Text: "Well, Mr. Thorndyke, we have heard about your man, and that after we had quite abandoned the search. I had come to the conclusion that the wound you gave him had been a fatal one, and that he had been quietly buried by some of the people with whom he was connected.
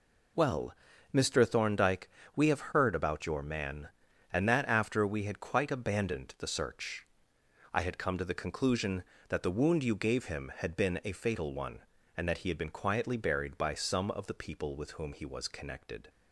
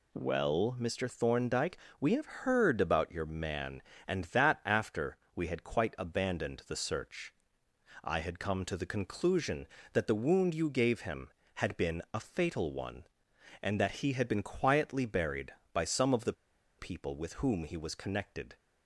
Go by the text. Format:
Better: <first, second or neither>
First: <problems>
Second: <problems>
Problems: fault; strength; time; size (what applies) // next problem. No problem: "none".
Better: first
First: none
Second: pauses between "after" and "we"; slight; at 5.1 s; 0.20 s long // pauses between "the" and "people"; at 16.3 s; 0.45 s long